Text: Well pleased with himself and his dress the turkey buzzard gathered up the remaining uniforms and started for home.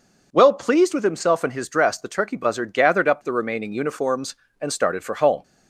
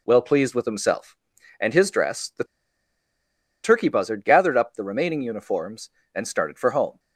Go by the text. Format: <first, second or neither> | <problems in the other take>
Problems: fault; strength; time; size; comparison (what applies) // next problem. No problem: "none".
first | pauses between "the" and "turkey"; at 2.4 s; 1.1 s long